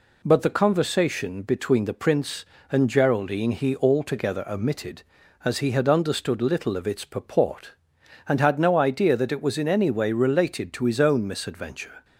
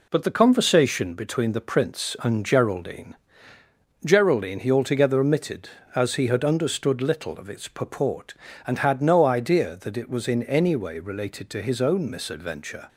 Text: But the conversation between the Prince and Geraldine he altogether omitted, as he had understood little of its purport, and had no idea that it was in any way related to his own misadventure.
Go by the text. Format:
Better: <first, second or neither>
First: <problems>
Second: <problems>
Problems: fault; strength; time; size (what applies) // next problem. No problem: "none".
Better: first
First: none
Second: says "Geraldine" twice; at 4.0 s